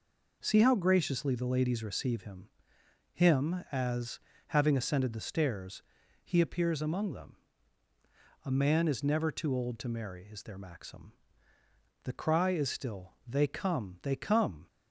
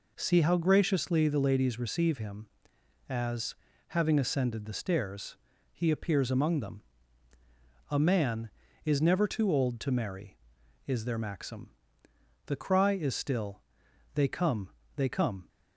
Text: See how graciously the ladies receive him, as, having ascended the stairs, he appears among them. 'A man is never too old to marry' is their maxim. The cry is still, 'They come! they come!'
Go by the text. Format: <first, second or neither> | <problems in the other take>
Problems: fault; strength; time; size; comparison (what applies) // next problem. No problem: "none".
second | says "him" twice; at 3.1 s